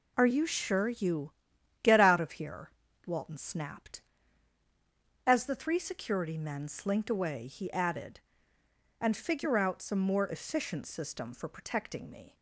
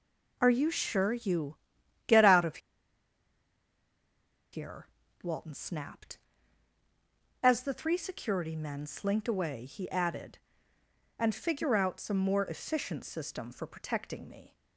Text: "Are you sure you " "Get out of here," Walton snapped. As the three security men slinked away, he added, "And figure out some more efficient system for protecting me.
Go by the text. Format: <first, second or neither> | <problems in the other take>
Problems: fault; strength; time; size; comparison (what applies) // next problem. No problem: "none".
first | pauses between "of" and "here"; strong; at 2.5 s; 1.9 s long